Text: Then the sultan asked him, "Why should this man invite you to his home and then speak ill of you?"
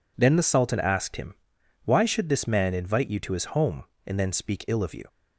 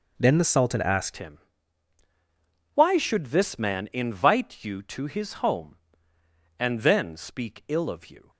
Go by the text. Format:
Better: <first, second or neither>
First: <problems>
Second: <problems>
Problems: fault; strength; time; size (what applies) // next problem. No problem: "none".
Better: first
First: none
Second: changes voice at "him"; from 1.1 s on; 7.1 s long